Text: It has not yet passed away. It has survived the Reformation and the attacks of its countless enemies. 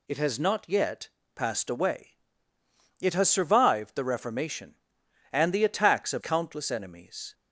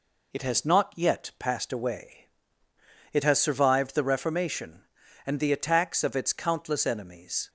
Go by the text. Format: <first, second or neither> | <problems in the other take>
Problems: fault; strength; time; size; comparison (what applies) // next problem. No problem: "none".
second | pauses between "yet" and "passed"; slight; at 1.0 s; 0.26 s long // skips "its"; at 6.2 s